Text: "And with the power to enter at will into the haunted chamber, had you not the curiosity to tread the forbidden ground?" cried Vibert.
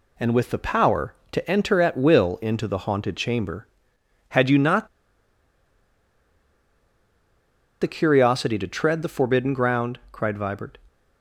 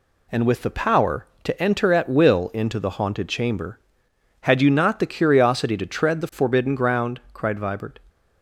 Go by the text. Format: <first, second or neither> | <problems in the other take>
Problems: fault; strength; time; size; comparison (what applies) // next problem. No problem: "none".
second | pauses between "not" and "the"; strong; at 4.8 s; 2.9 s long